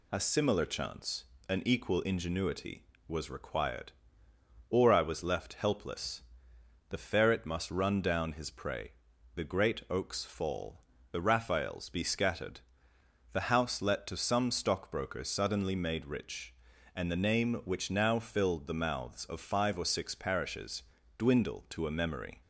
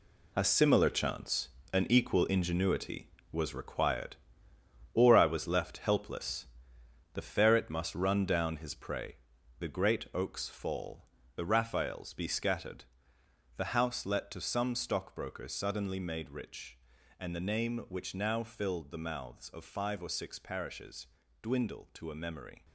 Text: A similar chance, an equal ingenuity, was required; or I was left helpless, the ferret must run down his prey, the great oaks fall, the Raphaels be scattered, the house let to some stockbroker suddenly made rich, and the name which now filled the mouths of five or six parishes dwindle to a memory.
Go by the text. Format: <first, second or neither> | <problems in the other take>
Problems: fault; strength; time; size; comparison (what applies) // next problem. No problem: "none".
first | gets quieter; strong; throughout; 9.5 dB // pauses between "parishes" and "dwindle"; at 21.0 s; 0.38 s long; also in the first